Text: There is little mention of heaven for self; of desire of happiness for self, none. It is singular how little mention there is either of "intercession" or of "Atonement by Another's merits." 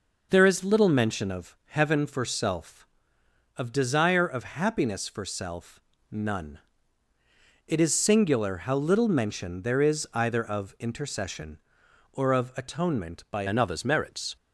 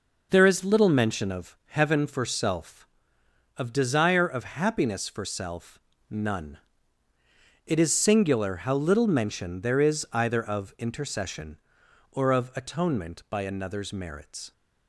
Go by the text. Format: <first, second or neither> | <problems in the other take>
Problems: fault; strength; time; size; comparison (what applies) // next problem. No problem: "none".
second | changes voice at "Another's"; from 13.4 s on; 0.9 s long